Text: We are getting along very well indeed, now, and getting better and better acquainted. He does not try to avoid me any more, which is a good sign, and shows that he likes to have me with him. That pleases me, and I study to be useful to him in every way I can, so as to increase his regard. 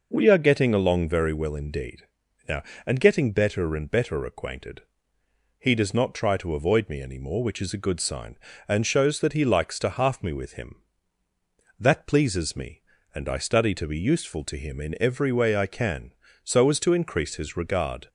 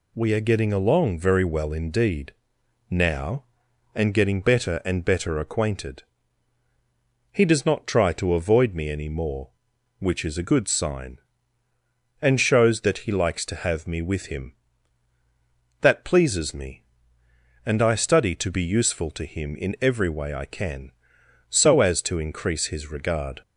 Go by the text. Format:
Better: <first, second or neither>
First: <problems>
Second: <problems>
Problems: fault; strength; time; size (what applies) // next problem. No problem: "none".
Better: second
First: says "half" for "have"; at 9.8 s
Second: none